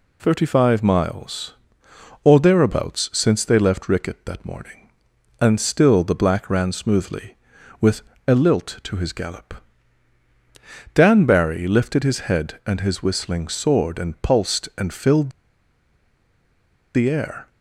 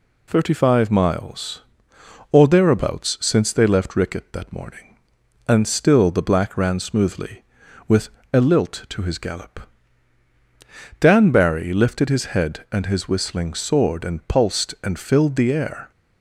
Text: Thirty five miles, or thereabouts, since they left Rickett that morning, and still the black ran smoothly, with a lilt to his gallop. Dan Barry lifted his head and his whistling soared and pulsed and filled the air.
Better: second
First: pauses between "with" and "a"; slight; at 8.0 s; 0.24 s long // pauses between "filled" and "the"; strong; at 15.3 s; 1.6 s long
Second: pauses between "with" and "a"; slight; at 8.1 s; 0.22 s long

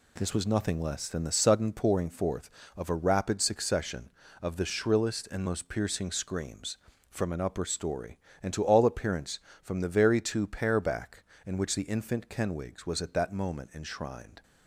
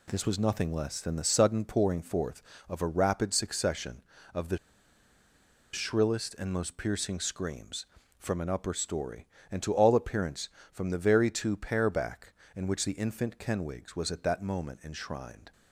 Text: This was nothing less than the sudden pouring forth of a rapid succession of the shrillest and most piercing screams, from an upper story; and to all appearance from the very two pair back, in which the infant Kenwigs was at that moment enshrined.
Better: first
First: none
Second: pauses between "the" and "shrillest"; at 4.5 s; 1.1 s long

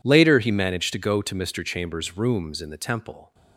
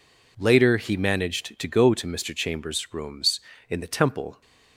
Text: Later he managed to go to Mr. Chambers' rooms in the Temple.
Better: neither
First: none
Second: none

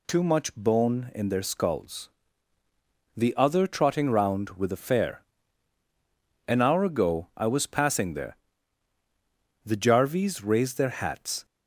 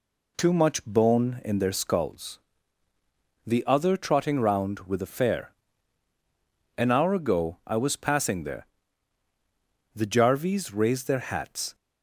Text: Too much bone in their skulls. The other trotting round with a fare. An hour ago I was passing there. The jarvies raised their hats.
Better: first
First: none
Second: starts louder than the rest; slight; until 2.2 s; 2.5 dB

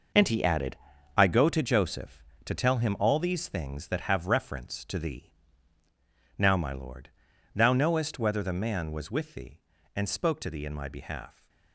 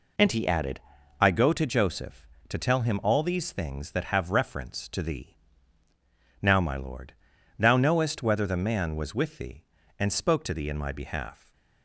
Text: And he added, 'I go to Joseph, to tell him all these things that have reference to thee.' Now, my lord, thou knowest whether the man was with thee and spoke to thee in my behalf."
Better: second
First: gets quieter; strong; throughout; 10 dB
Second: none

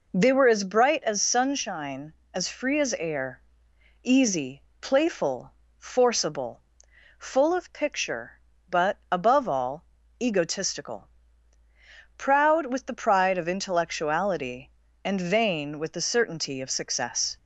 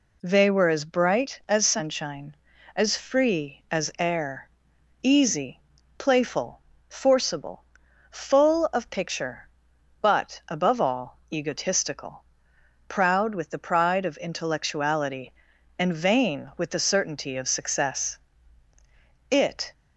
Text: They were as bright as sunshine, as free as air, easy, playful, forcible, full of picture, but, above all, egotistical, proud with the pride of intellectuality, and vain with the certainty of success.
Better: first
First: none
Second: goes on to say "It"; slight; from 19.2 s on; 0.42 s long

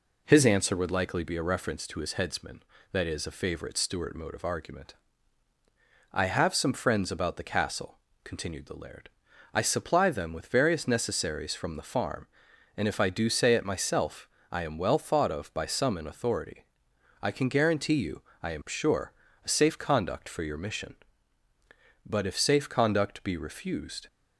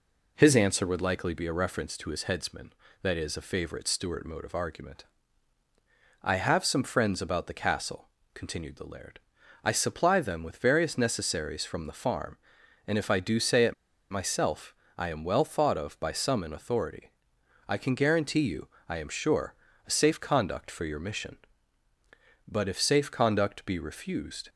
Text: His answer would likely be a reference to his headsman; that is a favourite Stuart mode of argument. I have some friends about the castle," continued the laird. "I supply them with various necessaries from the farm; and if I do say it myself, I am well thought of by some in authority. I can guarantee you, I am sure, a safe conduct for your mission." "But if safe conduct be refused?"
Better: first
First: none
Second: pauses between "it" and "myself"; at 13.7 s; 0.36 s long

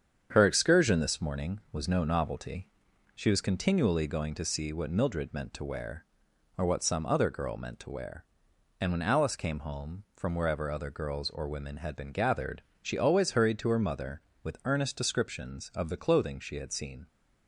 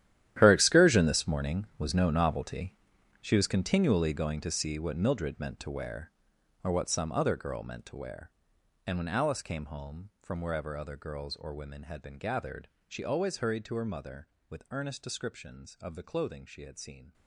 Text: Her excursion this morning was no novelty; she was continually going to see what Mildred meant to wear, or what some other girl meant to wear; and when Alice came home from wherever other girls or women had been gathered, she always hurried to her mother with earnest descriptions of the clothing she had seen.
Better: first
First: starts louder than the rest; strong; until 1.3 s; 8 dB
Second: gets quieter; strong; throughout; 16 dB // starts louder than the rest; strong; until 1.3 s; 12 dB

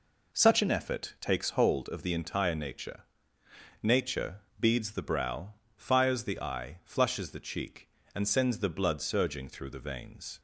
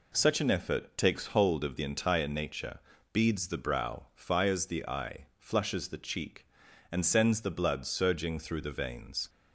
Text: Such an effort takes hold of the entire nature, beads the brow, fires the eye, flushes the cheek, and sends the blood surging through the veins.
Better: second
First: says "nature" twice; at 3.8 s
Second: none

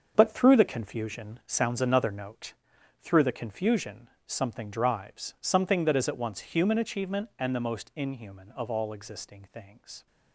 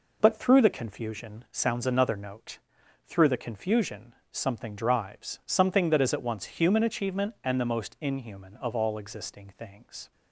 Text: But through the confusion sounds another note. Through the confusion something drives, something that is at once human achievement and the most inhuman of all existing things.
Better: second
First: gets quieter; strong; throughout; 9.5 dB // pauses between "confusion" and "something"; slight; at 4.0 s; 0.18 s long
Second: pauses between "confusion" and "something"; slight; at 4.1 s; 0.18 s long

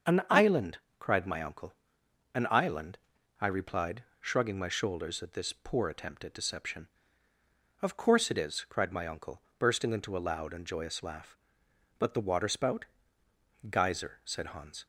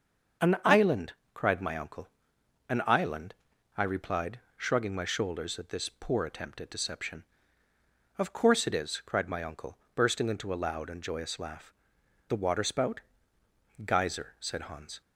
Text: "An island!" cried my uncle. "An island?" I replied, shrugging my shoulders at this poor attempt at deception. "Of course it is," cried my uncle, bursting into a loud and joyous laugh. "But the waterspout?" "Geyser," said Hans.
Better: first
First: starts louder than the rest; until 1.3 s; 6.5 dB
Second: starts louder than the rest; until 1.6 s; 6.5 dB // skips "But"; at 12.0 s

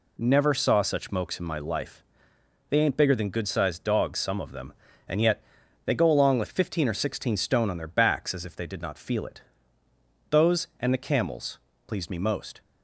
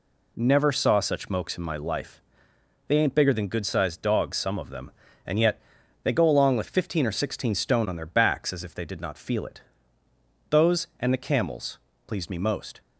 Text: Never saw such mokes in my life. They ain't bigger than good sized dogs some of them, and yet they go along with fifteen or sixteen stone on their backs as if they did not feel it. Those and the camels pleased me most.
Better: neither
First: pauses between "yet" and "they"; at 5.4 s; 0.42 s long // pauses between "camels" and "pleased"; slight; at 11.5 s; 0.28 s long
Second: pauses between "yet" and "they"; at 5.6 s; 0.42 s long // pauses between "camels" and "pleased"; slight; at 11.7 s; 0.28 s long

